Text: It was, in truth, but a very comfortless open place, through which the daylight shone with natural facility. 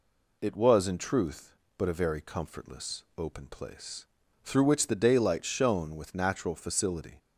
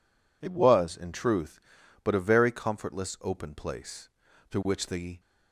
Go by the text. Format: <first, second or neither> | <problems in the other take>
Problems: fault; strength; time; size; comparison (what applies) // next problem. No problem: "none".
first | stops before "daylight shone with natural facility"; at 5.1 s